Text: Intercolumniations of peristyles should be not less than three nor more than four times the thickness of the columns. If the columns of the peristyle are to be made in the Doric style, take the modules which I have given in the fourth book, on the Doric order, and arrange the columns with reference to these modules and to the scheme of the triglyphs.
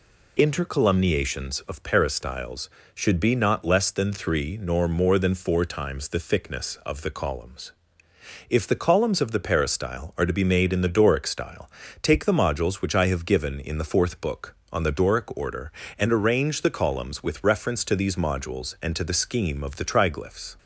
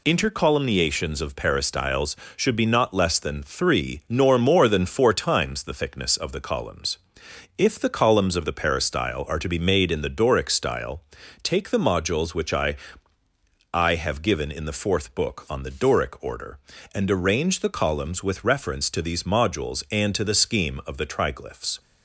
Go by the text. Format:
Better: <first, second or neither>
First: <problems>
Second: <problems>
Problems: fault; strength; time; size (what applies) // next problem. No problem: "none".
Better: first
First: none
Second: says "I" twice; at 13.7 s